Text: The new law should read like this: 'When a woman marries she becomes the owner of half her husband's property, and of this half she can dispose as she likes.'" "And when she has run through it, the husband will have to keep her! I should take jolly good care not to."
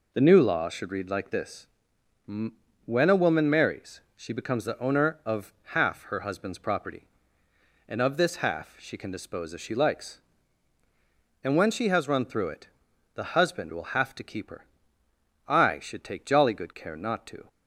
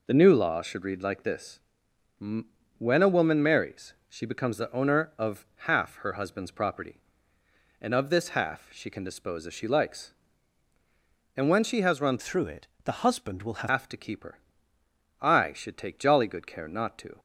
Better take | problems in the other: first | pauses between "marries" and "she"; slight; at 3.9 s; 0.16 s long; slight in the first // changes voice from "through" to "will"; from 12.1 to 13.6 s; 1.5 s long

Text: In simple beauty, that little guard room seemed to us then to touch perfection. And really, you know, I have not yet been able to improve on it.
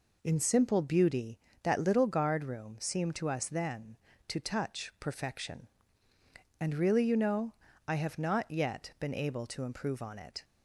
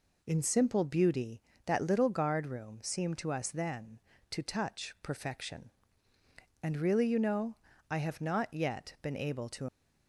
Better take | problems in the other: first | stops before "improve on it"; at 9.6 s

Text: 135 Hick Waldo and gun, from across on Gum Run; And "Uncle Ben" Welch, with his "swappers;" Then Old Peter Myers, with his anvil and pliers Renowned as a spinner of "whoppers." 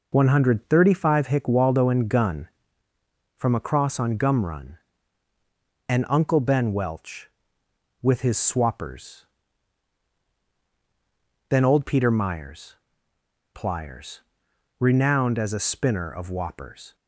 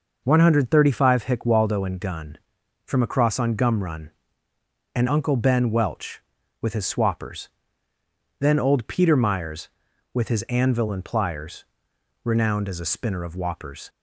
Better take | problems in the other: second | skips "with his anvil and"; at 13.1 s // pauses between "pliers" and "Renowned"; noticeable; at 14.1 s; 0.62 s long; noticeable in the second

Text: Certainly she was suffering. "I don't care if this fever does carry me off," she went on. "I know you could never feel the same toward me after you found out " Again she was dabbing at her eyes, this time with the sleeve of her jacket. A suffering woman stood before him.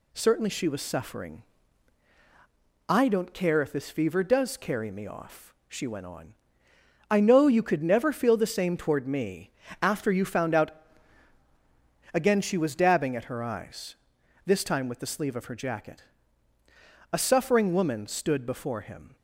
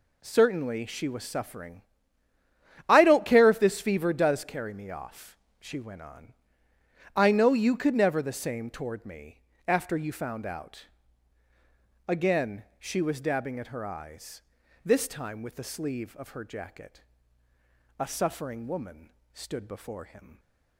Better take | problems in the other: first | skips "feel"; at 8.2 s // pauses between "me" and "after"; slight; at 9.4 s; 0.26 s long; slight in the first // pauses between "Again" and "she"; slight; at 12.6 s; 0.16 s long // pauses between "woman" and "stood"; slight; at 19.1 s; 0.22 s long

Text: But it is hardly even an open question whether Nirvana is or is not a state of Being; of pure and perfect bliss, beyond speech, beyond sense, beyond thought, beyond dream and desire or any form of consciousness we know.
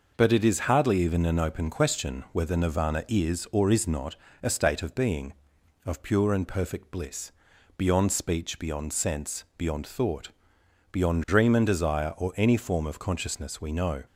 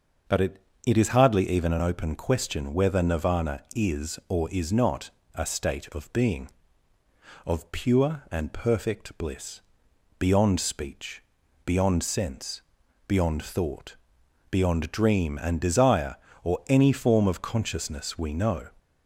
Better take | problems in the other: first | starts louder than the rest; until 1.5 s; 6.5 dB // says "it" twice; at 0.8 s // pauses between "not" and "a"; slight; at 5.0 s; 0.24 s long; slight in the first

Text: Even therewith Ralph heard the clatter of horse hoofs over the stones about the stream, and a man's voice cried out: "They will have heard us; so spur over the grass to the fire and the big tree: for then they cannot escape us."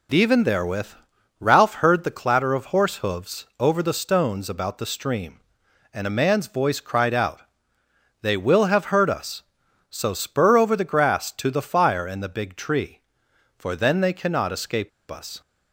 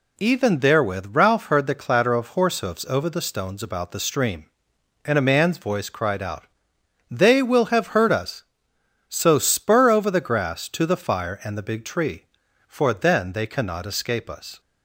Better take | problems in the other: second | pauses between "therewith" and "Ralph"; noticeable; at 0.8 s; 0.50 s long // pauses between "escape" and "us"; slight; at 14.8 s; 0.20 s long

